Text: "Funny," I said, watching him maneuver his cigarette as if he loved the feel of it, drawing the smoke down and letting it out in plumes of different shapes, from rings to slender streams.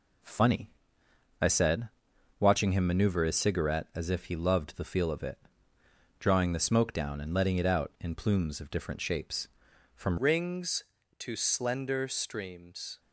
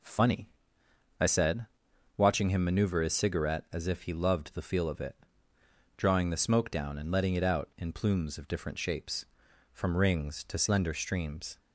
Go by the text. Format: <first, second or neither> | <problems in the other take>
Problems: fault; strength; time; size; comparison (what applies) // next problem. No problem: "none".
second | changes voice at "rings"; from 10.1 s on; 2.8 s long